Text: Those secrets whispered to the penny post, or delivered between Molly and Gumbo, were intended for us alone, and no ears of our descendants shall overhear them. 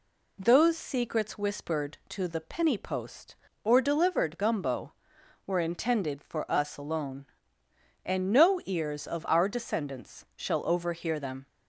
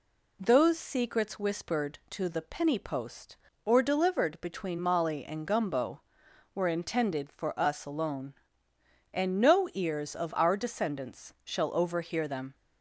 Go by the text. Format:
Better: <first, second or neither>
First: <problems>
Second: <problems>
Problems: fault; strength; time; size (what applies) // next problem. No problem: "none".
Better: second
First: skips "between Molly and"; at 4.3 s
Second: none